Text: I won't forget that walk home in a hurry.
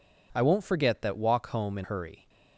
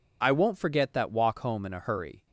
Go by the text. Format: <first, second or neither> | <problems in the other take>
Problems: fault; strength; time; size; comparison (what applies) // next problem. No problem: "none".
second | skips "a"; at 1.8 s